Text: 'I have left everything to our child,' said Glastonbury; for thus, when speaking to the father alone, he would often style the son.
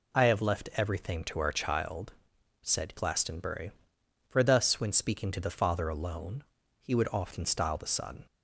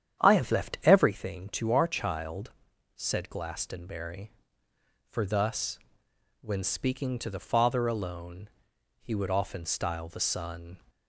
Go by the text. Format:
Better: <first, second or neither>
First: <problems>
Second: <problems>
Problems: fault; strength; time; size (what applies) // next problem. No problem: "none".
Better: first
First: none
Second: starts louder than the rest; strong; until 1.1 s; 9 dB